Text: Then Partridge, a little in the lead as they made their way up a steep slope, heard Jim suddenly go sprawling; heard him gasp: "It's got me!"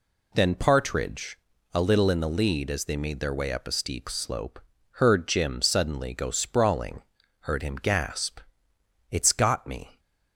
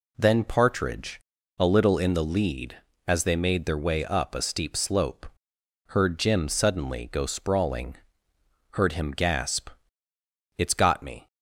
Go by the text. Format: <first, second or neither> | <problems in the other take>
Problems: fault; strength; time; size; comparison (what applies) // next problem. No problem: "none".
neither | none